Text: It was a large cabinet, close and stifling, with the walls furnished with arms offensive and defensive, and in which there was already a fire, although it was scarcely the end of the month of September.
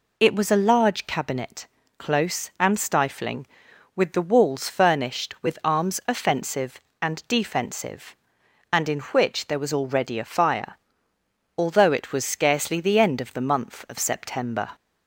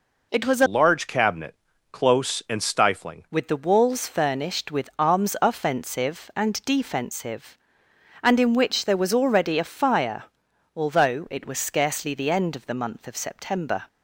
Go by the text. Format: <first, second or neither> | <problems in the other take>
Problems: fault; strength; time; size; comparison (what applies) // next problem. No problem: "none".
first | changes voice from "large" to "stifling"; from 0.6 to 3.2 s; 2.6 s long